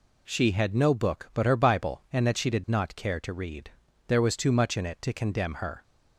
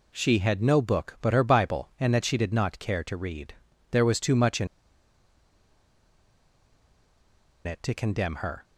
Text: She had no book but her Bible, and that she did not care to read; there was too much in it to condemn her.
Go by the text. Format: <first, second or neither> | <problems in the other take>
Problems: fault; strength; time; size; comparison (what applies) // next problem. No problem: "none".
first | pauses between "in" and "it"; strong; at 4.6 s; 2.9 s long